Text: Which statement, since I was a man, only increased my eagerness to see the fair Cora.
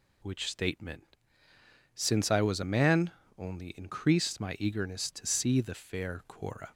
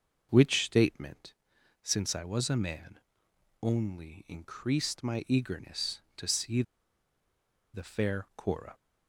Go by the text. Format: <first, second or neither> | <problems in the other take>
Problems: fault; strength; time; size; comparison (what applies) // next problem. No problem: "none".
first | pauses between "see" and "the"; at 6.6 s; 1.1 s long